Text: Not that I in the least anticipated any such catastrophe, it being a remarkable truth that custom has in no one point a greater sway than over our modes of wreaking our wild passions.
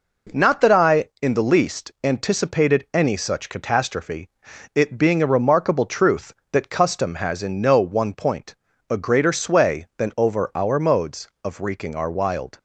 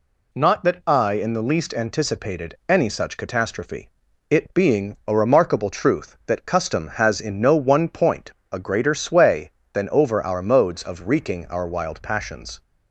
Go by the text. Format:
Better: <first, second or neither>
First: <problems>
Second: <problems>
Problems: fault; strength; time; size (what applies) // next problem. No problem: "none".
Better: second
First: pauses between "point" and "a"; slight; at 8.5 s; 0.36 s long // stops before "passions"; at 12.5 s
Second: pauses between "point" and "a"; slight; at 8.3 s; 0.18 s long